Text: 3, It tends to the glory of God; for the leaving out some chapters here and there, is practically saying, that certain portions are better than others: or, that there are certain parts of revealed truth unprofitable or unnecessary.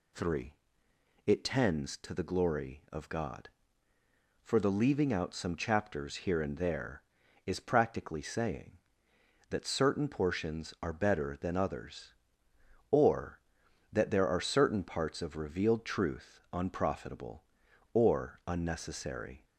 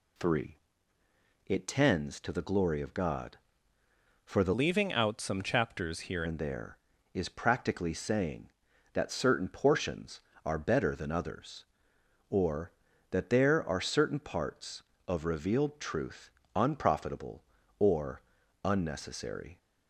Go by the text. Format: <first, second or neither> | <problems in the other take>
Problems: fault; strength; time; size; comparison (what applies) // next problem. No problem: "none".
first | changes voice from "leaving" to "here"; from 4.5 to 6.2 s; 1.7 s long // pauses between "truth" and "unprofitable"; slight; at 16.2 s; 0.26 s long // pauses between "or" and "unnecessary"; at 18.2 s; 0.42 s long